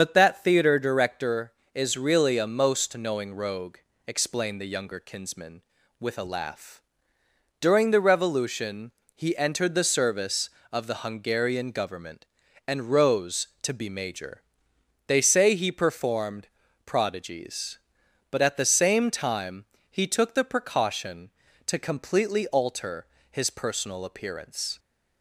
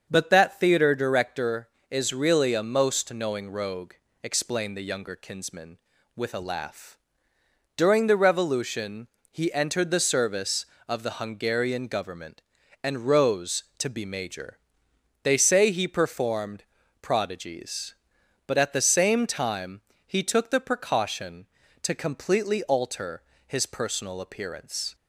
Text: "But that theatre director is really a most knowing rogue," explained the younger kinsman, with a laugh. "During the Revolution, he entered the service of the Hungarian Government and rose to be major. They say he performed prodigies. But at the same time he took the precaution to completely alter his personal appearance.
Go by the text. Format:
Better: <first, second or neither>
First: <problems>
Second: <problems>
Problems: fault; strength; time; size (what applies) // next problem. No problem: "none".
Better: second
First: loses the start of "But"; at 0.0 s; 65 ms // starts louder than the rest; until 1.0 s; 6.5 dB // pauses between "performed" and "prodigies"; at 16.4 s; 0.40 s long // pauses between "time" and "he"; slight; at 19.6 s; 0.24 s long // pauses between "alter" and "his"; slight; at 23.0 s; 0.26 s long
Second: starts louder than the rest; until 1.1 s; 7 dB // pauses between "performed" and "prodigies"; at 16.6 s; 0.40 s long // pauses between "time" and "he"; slight; at 19.8 s; 0.24 s long // pauses between "alter" and "his"; slight; at 23.2 s; 0.26 s long